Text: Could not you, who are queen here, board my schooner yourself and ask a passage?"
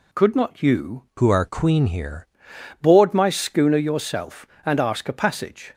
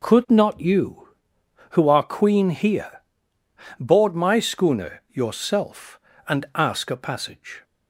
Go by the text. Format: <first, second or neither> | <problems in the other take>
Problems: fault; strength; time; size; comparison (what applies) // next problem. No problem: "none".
second | changes voice from "who" to "here"; from 1.1 to 2.2 s; 1.1 s long